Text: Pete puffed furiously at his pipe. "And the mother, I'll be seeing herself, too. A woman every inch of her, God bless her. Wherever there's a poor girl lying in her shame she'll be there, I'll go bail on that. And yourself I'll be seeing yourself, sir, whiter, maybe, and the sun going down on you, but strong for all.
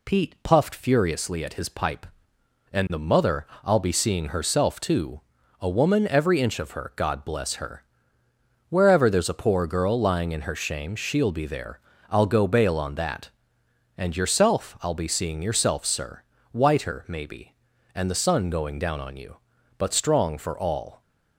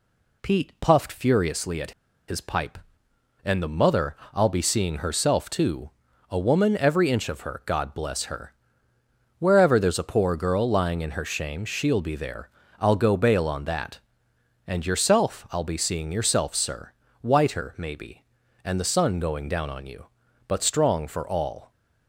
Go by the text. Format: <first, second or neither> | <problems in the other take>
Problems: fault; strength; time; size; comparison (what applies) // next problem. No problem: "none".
first | pauses between "at" and "his"; at 1.9 s; 0.36 s long